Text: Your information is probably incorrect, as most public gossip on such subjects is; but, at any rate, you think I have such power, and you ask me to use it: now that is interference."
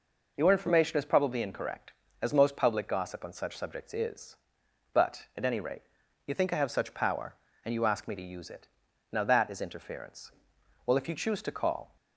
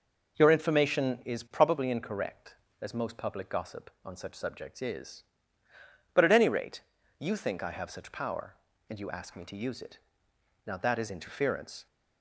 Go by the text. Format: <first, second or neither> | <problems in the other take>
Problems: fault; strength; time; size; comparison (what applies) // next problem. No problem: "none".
second | goes on to say "Well if you choose to call"; noticeable; from 10.8 s on; 1.1 s long